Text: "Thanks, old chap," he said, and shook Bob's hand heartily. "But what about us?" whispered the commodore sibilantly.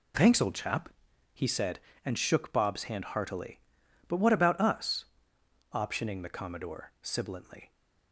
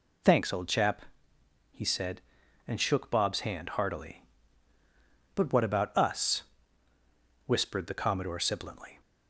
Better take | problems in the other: second | says "optioning" for "whispered"; at 5.7 s

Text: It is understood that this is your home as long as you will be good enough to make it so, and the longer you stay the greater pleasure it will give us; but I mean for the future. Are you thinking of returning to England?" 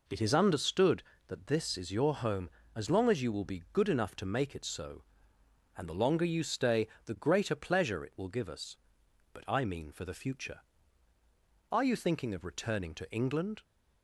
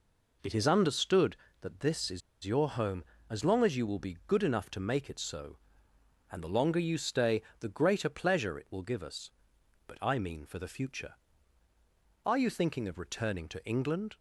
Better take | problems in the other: first | pauses between "is" and "your"; slight; at 2.2 s; 0.23 s long // pauses between "stay" and "the"; slight; at 7.4 s; 0.20 s long; slight in the first

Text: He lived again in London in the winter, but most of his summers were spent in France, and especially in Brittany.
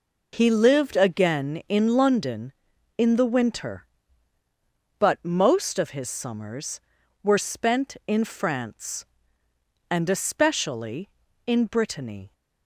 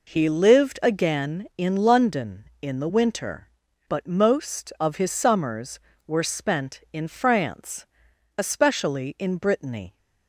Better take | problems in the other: first | skips "and"; at 8.1 s

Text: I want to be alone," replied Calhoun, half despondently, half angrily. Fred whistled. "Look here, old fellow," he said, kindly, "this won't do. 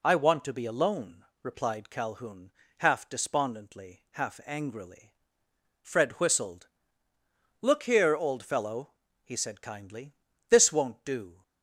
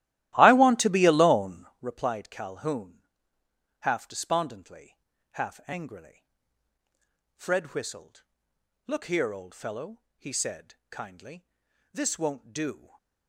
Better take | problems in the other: first | starts louder than the rest; strong; until 1.8 s; 14.5 dB // stays silent after the last word; slight; from 12.7 s on; 0.5 s long

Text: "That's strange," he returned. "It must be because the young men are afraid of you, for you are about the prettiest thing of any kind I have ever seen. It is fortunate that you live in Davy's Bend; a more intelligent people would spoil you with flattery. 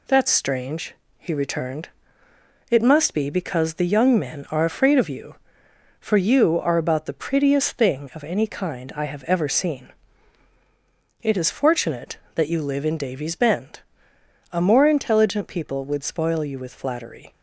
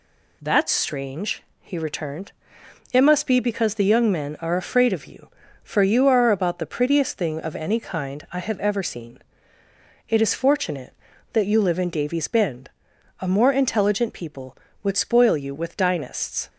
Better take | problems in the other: first | says "dynasts" for "flattery"; at 15.7 s

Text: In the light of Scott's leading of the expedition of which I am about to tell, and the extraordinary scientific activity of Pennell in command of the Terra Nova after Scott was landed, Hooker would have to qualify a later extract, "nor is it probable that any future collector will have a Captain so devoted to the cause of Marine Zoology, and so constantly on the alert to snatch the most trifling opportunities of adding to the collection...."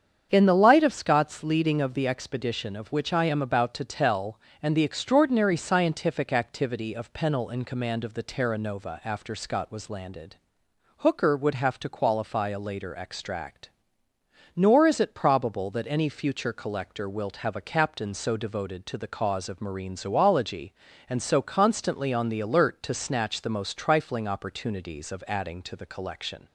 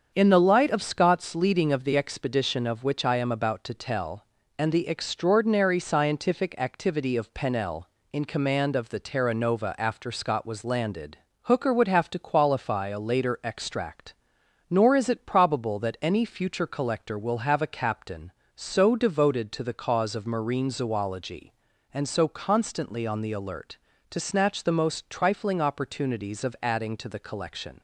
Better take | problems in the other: second | starts louder than the rest; strong; until 1.3 s; 7.5 dB; strong in the second // says "wilt" for "will"; at 17.0 s

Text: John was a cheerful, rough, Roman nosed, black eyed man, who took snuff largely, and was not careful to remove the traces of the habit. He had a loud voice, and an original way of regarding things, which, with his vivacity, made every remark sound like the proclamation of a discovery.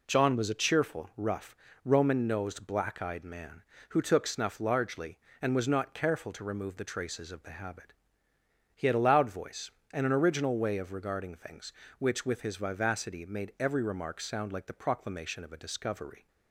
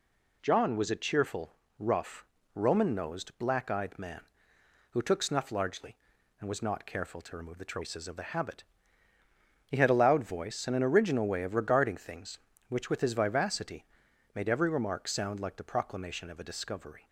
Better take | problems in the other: neither | none

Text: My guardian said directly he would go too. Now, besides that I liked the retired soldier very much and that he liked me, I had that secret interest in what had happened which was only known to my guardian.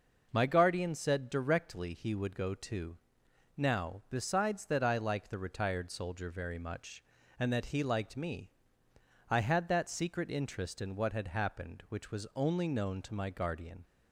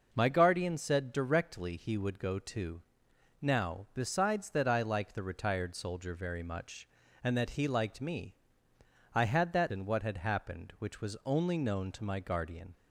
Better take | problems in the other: first | skips "secret interest"; at 9.7 s

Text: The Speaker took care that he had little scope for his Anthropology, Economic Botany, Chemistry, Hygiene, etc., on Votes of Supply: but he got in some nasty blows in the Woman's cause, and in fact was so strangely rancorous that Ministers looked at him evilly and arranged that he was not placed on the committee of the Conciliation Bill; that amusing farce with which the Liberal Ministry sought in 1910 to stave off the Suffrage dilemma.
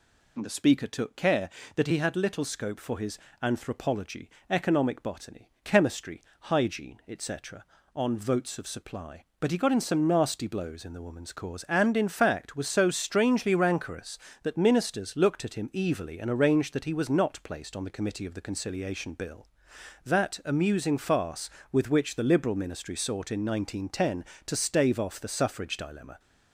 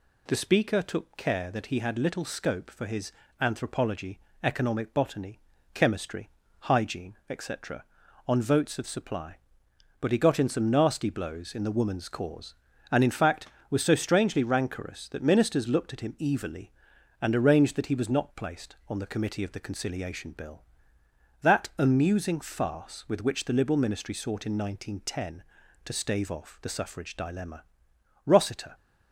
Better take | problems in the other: first | pauses between "his" and "Anthropology"; slight; at 3.1 s; 0.28 s long; slight in the first // goes on to say "Rossiter"; from 28.2 s on; 0.50 s long

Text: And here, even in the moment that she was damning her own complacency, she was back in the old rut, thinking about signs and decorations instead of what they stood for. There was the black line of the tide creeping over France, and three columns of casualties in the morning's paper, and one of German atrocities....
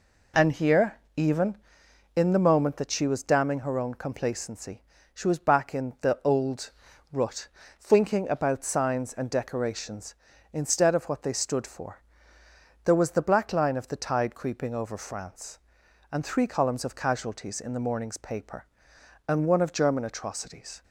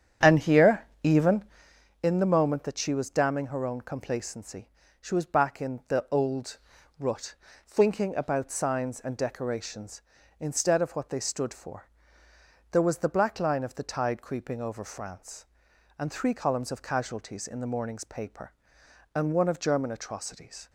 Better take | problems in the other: first | starts louder than the rest; strong; until 1.9 s; 9 dB // pauses between "old" and "rut"; at 6.5 s; 0.42 s long; also in the first

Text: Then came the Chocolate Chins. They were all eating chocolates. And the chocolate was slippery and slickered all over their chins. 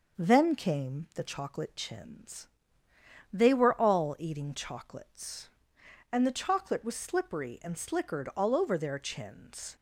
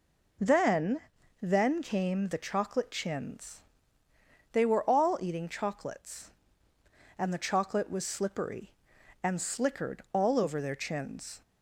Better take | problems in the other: first | says "Then" twice; at 1.4 s

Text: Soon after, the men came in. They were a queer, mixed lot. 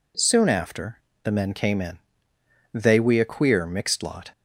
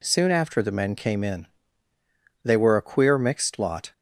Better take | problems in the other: second | says "we" for "were"; at 2.9 s

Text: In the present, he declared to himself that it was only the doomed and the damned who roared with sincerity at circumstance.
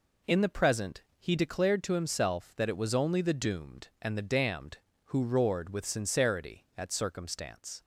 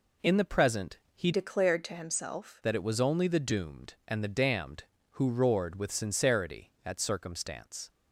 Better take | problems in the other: first | changes voice from "declared" to "himself"; from 1.3 to 2.6 s; 1.3 s long

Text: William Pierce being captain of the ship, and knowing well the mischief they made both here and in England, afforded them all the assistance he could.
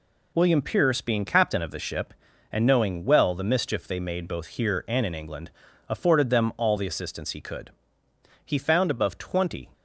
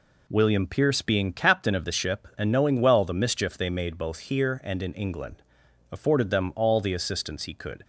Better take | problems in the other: second | goes on to say "He found above twenty"; noticeable; from 8.4 s on; 1.2 s long

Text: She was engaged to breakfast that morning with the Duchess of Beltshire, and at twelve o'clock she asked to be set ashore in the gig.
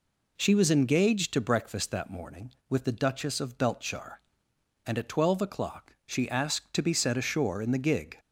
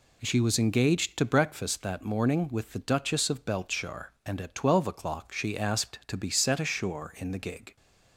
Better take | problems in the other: neither | none

